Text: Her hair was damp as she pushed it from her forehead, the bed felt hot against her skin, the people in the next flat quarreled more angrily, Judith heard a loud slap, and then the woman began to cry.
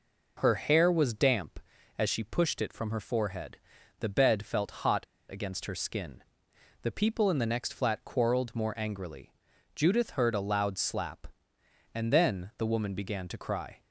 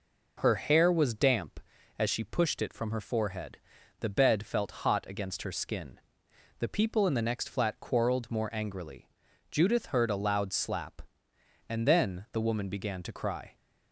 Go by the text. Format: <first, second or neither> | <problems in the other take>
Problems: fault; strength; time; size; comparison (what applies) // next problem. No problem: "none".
second | pauses between "hot" and "against"; slight; at 5.0 s; 0.27 s long